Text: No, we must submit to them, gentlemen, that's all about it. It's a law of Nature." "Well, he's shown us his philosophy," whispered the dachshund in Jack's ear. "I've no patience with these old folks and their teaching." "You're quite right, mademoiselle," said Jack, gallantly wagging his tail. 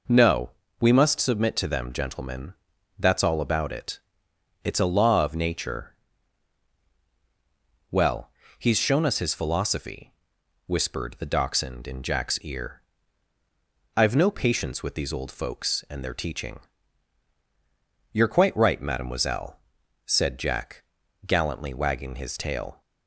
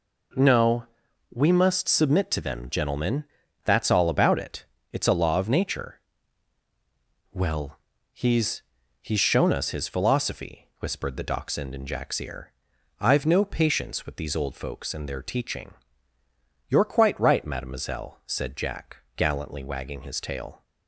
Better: first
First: none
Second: says "he's" twice; at 9.0 s

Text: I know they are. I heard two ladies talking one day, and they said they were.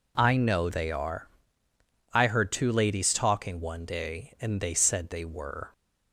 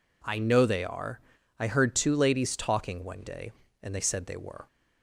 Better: neither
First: none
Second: none

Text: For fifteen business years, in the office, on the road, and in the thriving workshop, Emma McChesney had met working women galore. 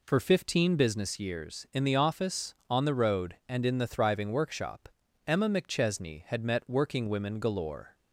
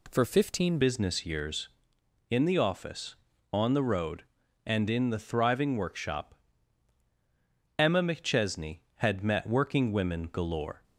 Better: first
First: none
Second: changes voice at "business"; from 0.7 s on; 10.1 s long

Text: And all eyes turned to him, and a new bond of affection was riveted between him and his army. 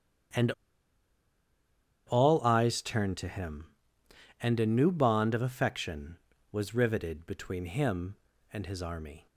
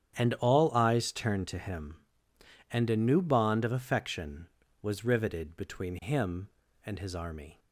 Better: second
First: starts louder than the rest; strong; until 2.9 s; 10 dB // pauses between "And" and "all"; strong; at 0.4 s; 1.5 s long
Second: starts louder than the rest; strong; until 1.2 s; 9.5 dB

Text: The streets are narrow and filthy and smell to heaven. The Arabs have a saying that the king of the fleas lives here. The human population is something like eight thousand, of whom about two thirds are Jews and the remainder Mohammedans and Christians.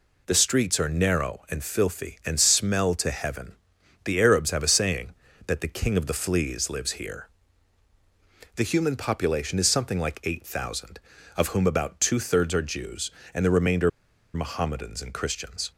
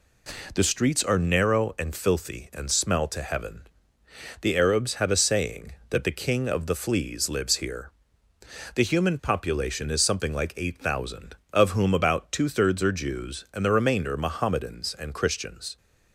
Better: second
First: pauses between "remainder" and "Mohammedans"; at 13.9 s; 0.44 s long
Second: none

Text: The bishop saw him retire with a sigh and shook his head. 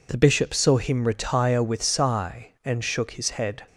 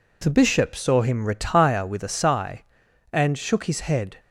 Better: second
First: skips "a"; at 1.8 s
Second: none

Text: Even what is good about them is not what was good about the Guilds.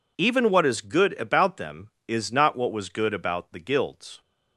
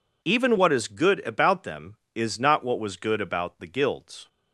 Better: neither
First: none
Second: none

